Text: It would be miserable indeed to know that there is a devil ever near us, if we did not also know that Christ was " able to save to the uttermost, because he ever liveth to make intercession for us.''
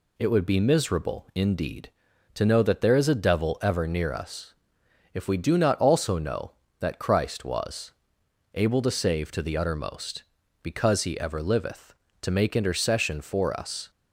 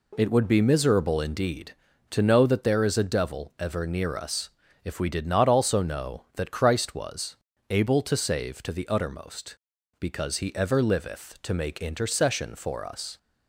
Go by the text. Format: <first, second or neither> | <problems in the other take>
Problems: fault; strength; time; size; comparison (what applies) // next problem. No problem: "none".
second | says "do" for "did"; at 5.3 s